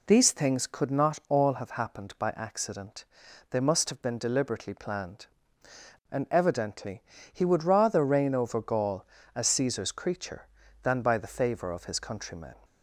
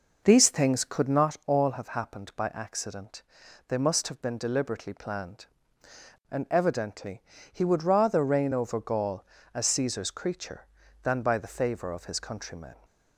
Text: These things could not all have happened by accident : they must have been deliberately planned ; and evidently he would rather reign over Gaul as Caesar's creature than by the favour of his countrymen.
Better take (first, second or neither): first